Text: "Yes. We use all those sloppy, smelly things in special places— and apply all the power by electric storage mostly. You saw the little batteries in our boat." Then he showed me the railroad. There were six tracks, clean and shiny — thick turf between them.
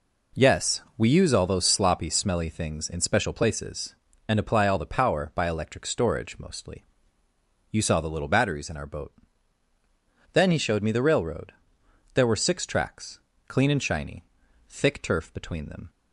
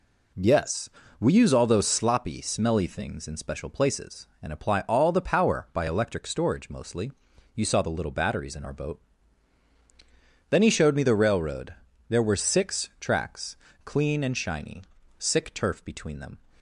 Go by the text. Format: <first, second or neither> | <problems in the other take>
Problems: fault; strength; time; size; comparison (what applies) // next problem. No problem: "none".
first | says "sick" for "thick"; at 15.1 s